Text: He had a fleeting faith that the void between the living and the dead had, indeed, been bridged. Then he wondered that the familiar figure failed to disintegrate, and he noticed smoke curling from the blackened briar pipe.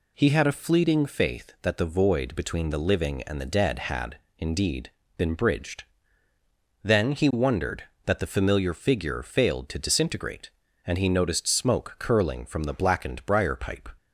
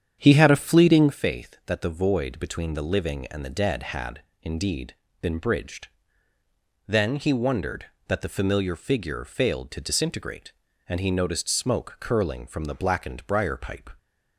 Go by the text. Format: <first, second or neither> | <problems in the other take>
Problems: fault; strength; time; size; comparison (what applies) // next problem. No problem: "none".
first | starts louder than the rest; strong; until 1.2 s; 8.5 dB